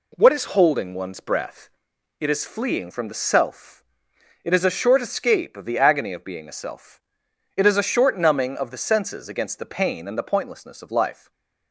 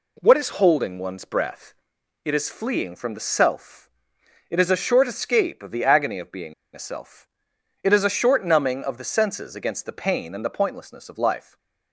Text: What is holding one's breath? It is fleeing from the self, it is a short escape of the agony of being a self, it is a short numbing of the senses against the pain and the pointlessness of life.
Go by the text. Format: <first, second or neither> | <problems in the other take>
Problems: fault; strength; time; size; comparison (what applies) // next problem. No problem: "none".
first | pauses between "being" and "a"; slight; at 6.5 s; 0.21 s long // stays silent after the last word; slight; from 11.4 s on; 0.5 s long; slight in the first